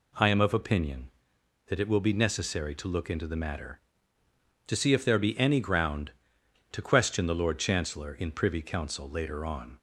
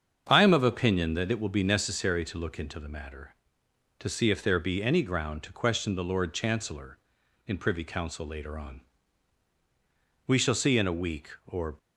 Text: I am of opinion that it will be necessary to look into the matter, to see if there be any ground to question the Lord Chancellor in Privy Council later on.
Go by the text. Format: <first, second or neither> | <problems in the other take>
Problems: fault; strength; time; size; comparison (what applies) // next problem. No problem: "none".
first | starts louder than the rest; strong; until 1.3 s; 7 dB // goes on to say "We shall see in a week or"; from 10.2 s on; 1.5 s long